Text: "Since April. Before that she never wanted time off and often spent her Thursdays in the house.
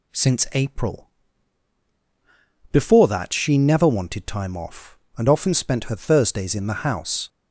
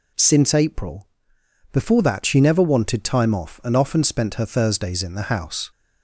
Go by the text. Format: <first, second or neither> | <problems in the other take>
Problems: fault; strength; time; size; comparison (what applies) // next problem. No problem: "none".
neither | none